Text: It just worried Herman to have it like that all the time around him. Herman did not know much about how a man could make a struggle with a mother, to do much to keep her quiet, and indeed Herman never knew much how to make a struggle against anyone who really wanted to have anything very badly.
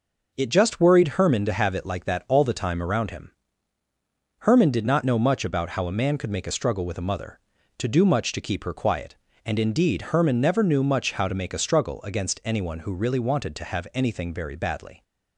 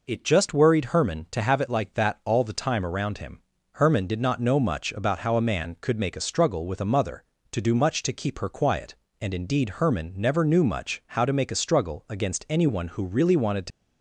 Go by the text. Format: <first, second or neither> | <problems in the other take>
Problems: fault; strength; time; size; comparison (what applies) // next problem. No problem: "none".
first | stops before "have anything very badly"; at 13.7 s